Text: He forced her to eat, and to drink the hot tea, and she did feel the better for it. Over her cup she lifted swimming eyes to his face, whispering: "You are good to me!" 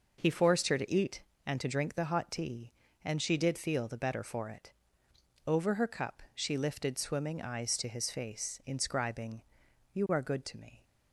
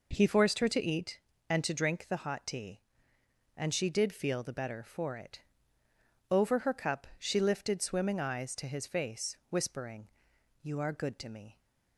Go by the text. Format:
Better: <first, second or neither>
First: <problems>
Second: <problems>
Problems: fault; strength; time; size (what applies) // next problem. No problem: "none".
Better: second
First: says "inscribing" for "whispering"; at 8.6 s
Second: none